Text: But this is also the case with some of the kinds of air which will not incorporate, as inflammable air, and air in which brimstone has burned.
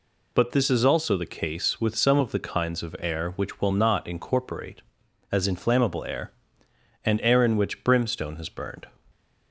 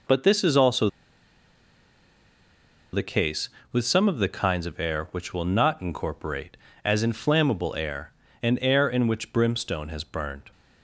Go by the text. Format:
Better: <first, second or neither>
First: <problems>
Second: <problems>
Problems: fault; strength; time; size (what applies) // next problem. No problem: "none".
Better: first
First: none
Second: pauses between "also" and "the"; strong; at 0.8 s; 2.0 s long